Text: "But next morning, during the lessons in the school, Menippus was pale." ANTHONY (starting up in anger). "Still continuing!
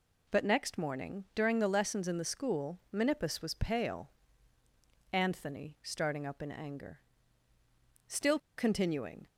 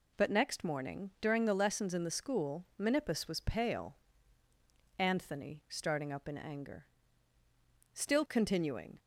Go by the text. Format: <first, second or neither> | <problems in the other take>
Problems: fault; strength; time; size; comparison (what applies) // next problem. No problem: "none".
second | pauses between "Still" and "continuing"; slight; at 8.3 s; 0.20 s long